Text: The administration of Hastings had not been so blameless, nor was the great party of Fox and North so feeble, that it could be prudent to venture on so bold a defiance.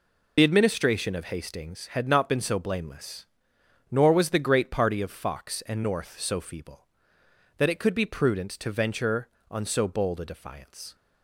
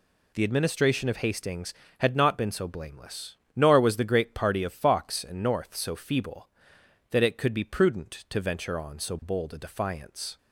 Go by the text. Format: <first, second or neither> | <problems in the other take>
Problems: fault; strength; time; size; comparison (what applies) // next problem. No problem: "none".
second | loses the start of "The"; at 0.3 s; 35 ms